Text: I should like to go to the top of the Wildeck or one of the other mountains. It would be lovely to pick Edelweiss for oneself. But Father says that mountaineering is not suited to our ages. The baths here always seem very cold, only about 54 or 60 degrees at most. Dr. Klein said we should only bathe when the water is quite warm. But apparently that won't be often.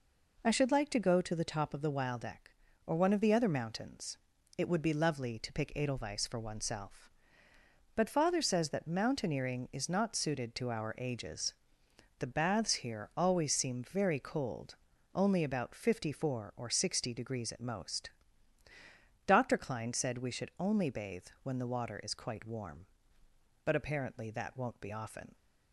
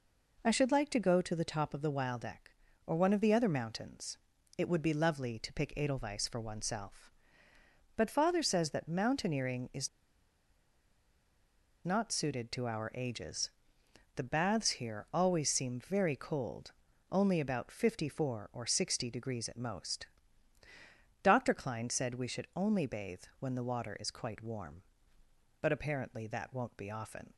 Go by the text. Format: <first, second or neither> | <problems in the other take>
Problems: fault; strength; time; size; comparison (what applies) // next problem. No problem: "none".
first | pauses between "is" and "not"; strong; at 9.8 s; 1.9 s long // pauses between "bathe" and "when"; slight; at 23.2 s; 0.18 s long; slight in the first